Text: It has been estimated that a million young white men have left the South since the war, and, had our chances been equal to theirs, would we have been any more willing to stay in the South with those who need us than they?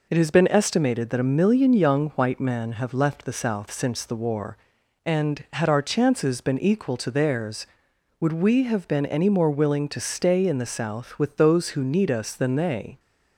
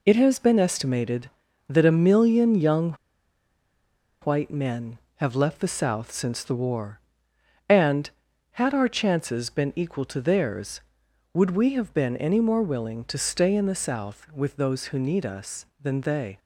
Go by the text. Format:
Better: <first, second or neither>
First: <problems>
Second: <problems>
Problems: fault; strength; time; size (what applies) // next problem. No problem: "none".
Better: first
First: none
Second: pauses between "young" and "white"; strong; at 2.9 s; 1.2 s long